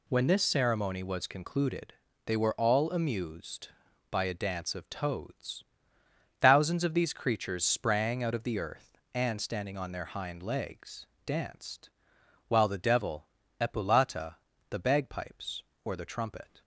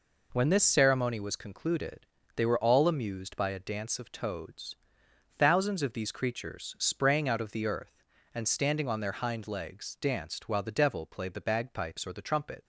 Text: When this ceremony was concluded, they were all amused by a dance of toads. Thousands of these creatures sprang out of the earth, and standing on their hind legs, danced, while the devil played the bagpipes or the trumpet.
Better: second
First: says "epulata" for "played"; at 13.5 s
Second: none

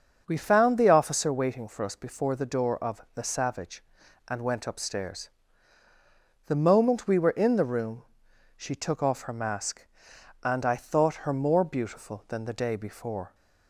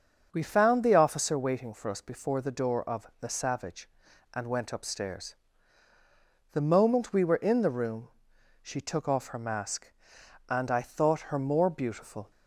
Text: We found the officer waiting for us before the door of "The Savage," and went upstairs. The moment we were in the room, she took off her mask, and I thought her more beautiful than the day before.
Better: first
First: starts louder than the rest; until 1.2 s; 6.5 dB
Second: starts louder than the rest; until 1.3 s; 6.5 dB // stops before "than the day before"; at 12.3 s

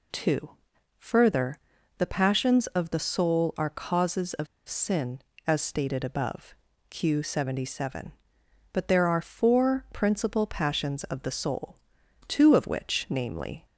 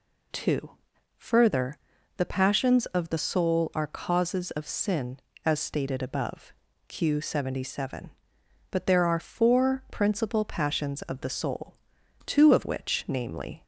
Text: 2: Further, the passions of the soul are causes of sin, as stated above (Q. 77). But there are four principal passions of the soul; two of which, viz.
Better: second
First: pauses between "of" and "sin"; slight; at 4.4 s; 0.21 s long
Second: none

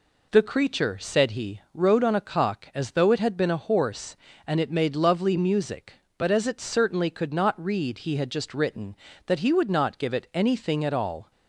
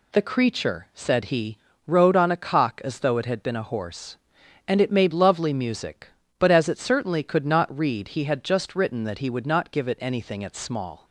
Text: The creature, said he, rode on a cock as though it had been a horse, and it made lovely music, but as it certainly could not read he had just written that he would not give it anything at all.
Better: first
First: none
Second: says "small" for "all"; at 10.5 s

